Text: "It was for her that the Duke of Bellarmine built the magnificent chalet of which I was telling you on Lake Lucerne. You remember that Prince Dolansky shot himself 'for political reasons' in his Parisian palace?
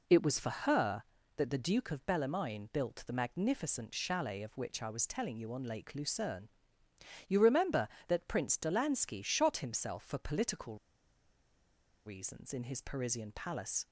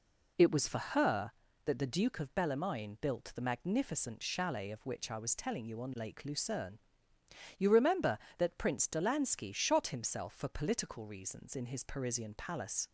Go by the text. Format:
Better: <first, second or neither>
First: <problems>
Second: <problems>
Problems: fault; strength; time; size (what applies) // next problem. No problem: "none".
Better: second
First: pauses between "political" and "reasons"; strong; at 10.7 s; 1.3 s long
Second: none